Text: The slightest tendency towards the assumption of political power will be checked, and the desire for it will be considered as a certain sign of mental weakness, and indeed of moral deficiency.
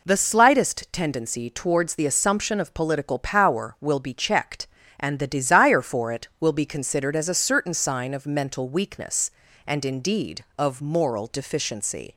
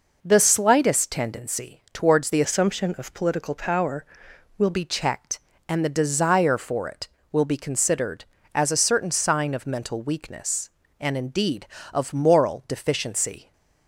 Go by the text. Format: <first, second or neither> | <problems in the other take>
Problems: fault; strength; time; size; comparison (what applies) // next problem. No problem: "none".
first | changes voice from "assumption" to "will"; from 2.4 to 4.7 s; 2.3 s long